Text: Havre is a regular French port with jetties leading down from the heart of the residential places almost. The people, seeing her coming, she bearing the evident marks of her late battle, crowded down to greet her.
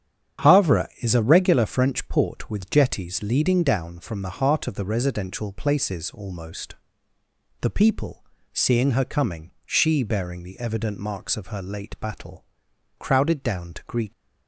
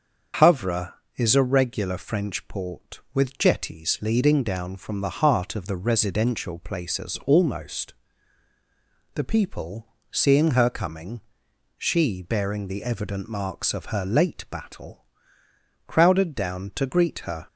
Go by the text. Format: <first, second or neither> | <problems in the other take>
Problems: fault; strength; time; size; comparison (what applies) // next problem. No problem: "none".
second | starts louder than the rest; strong; until 1.5 s; 9 dB; also in the second // stops before "her"; at 14.1 s